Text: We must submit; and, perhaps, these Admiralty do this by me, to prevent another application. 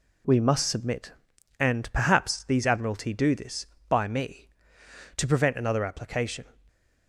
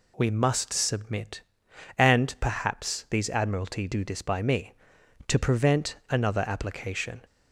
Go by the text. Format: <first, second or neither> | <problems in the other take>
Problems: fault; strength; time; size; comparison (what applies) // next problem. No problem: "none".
neither | none